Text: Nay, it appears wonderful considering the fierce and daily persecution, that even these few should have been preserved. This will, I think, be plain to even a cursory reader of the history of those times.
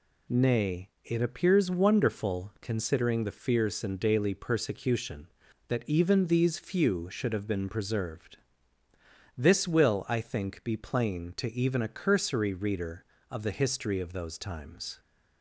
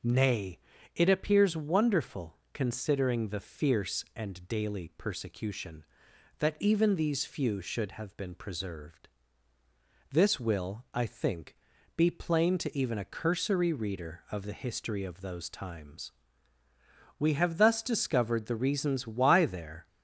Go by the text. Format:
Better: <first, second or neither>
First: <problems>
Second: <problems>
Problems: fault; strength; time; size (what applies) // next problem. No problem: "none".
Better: first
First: none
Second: pauses between "wonderful" and "considering"; slight; at 2.3 s; 0.16 s long // goes on to say "We have thus discovered the reasons why there"; strong; from 17.1 s on; 2.7 s long